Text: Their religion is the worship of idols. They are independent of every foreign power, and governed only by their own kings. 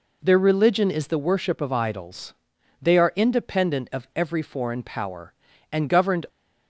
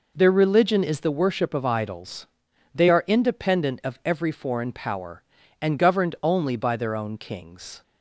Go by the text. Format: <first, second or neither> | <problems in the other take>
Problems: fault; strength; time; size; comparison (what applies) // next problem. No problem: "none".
second | stops before "only by their own kings"; at 6.2 s